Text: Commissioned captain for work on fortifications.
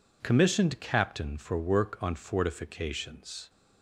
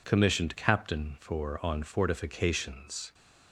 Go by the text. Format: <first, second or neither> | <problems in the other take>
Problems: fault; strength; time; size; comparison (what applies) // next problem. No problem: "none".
first | skips "work"; at 1.6 s